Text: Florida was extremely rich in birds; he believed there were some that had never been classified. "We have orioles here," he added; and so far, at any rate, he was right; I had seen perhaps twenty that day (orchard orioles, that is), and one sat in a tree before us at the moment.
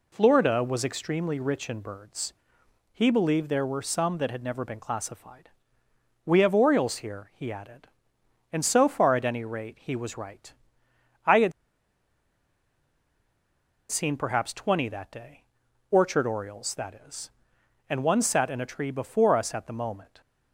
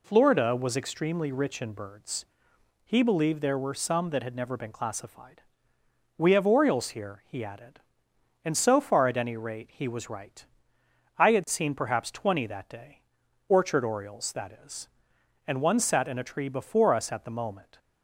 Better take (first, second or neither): second